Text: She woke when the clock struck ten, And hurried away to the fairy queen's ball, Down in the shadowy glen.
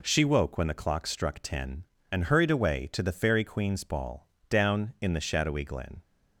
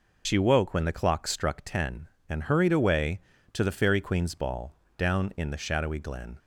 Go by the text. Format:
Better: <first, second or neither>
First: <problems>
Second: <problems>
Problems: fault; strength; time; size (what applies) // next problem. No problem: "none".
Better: first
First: none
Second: loses the start of "She"; at 0.2 s; 100 ms